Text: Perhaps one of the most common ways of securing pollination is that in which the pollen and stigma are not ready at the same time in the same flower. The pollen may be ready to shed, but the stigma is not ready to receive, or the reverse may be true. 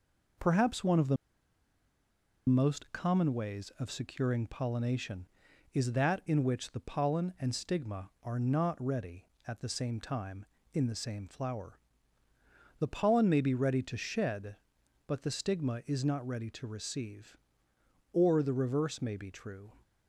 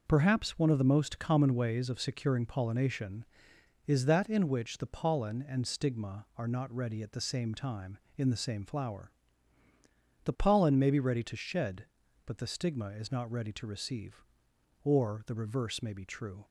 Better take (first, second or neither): second